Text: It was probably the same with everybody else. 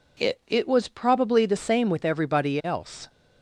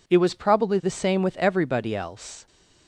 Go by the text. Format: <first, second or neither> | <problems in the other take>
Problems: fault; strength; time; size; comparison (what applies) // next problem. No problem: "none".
second | says "It" twice; at 0.4 s